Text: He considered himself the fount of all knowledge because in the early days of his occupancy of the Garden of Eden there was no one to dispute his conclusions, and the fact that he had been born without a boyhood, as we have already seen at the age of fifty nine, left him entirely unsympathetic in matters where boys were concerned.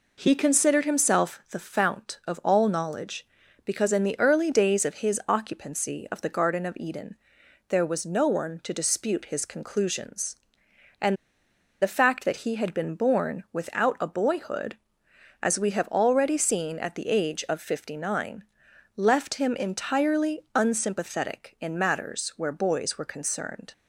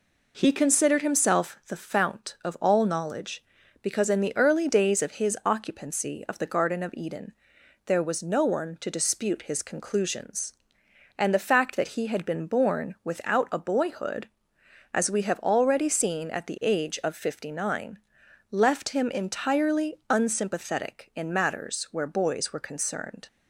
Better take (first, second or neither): second